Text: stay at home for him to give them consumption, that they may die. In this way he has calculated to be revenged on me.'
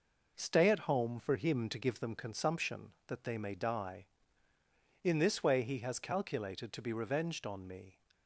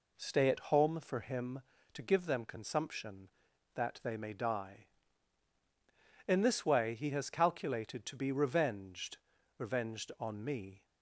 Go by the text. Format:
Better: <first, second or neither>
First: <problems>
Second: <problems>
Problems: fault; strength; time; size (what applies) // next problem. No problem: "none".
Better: first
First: none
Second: says "revenged" twice; at 9.5 s